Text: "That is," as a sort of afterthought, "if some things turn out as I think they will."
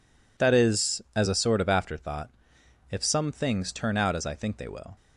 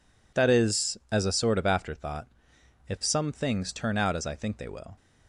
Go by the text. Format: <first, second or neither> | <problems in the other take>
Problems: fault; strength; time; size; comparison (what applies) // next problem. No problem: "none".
neither | none